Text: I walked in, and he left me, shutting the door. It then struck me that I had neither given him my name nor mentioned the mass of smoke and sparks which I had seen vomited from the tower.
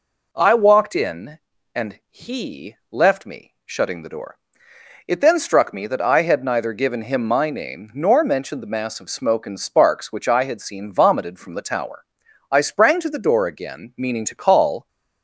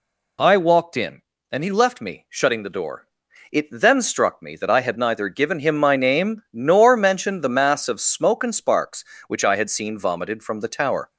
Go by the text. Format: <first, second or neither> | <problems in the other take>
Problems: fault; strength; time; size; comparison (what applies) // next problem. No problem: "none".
second | goes on to say "I sprang to the door again meaning to call"; strong; from 12.5 s on; 2.3 s long